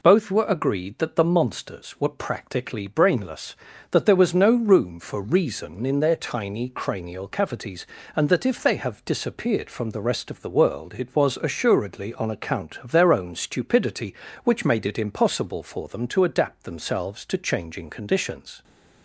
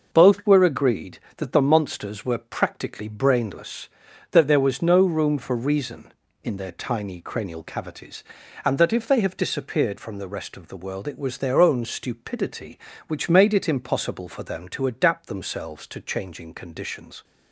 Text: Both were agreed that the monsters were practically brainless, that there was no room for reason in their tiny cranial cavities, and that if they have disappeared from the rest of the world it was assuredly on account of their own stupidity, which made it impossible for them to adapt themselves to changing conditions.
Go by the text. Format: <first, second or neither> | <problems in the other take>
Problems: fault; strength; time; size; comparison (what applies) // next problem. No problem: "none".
first | skips "assuredly on account of"; at 11.3 s